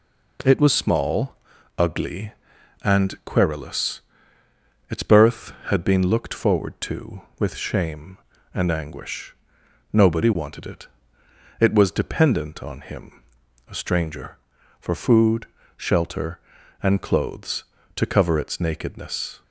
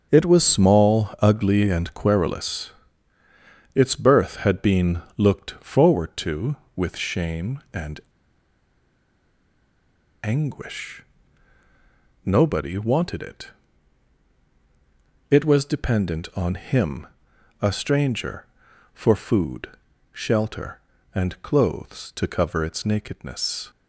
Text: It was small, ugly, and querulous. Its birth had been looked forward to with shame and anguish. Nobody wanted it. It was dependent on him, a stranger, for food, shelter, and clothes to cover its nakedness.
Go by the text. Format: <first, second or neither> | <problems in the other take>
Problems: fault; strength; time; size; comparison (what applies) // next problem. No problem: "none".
first | starts louder than the rest; until 1.1 s; 7 dB // pauses between "been" and "looked"; slight; at 5.0 s; 0.16 s long // pauses between "and" and "anguish"; strong; at 8.0 s; 2.2 s long